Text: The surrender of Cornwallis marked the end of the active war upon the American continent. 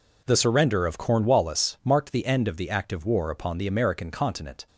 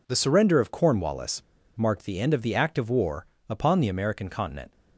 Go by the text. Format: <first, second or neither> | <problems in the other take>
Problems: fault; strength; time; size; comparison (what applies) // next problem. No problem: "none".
first | pauses between "Cornwallis" and "marked"; slight; at 1.4 s; 0.33 s long // pauses between "war" and "upon"; slight; at 3.2 s; 0.24 s long